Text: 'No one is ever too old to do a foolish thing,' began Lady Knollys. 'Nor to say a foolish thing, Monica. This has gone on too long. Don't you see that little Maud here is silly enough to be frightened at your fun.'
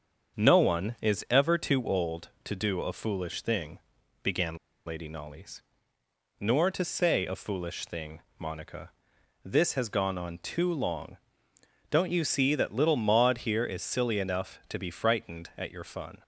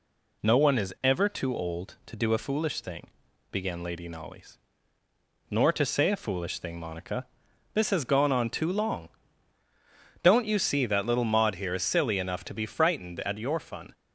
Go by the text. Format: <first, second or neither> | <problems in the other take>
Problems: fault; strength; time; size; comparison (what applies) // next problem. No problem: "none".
second | starts louder than the rest; until 1.4 s; 7 dB // pauses between "began" and "Lady"; slight; at 4.5 s; 0.28 s long